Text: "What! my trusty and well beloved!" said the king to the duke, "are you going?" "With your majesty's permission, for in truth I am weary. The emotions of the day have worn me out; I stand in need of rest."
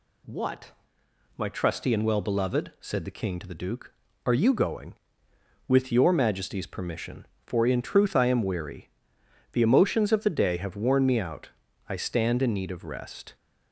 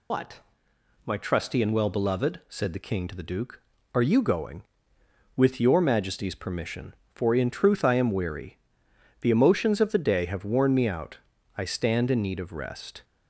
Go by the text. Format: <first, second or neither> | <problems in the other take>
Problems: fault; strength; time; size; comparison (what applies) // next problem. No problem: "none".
first | loses the start of "What"; at 0.1 s; 175 ms